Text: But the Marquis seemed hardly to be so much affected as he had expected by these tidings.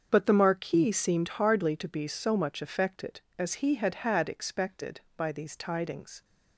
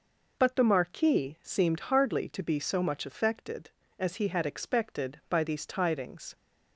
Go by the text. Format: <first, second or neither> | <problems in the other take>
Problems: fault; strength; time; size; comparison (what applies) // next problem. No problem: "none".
second | starts louder than the rest; until 1.1 s; 7 dB // says "had" twice; at 3.9 s